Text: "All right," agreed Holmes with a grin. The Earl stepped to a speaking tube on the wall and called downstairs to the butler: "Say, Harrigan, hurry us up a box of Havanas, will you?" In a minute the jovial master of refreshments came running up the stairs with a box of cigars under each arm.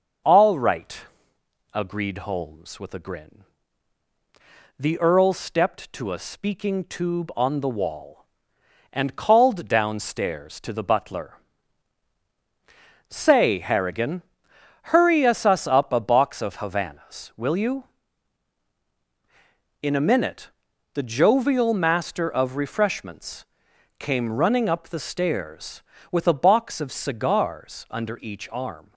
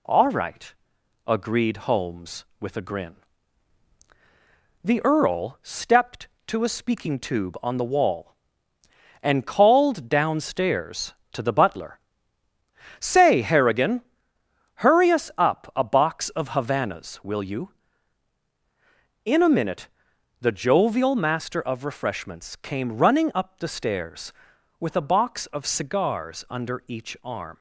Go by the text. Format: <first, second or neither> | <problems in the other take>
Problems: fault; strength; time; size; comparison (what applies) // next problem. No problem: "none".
second | says "us" twice; at 15.4 s // pauses between "minute" and "the"; at 20.5 s; 0.42 s long; noticeable in the second // pauses between "refreshments" and "came"; noticeable; at 23.4 s; 0.56 s long